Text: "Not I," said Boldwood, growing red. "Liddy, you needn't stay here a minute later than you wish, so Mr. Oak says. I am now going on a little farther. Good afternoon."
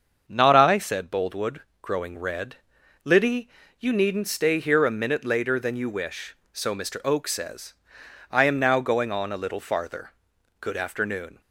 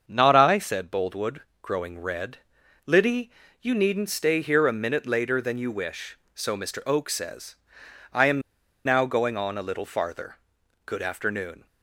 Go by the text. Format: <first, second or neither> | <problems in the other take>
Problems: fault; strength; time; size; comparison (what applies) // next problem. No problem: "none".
first | starts louder than the rest; until 1.0 s; 6.5 dB; also in the first // pauses between "am" and "now"; at 8.4 s; 0.43 s long